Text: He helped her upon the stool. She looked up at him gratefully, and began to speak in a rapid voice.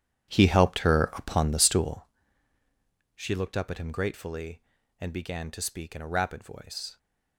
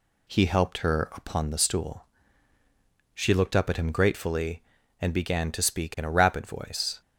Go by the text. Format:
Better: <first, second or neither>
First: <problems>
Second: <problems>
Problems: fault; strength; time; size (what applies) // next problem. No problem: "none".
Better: second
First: starts louder than the rest; strong; until 2.2 s; 10 dB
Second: none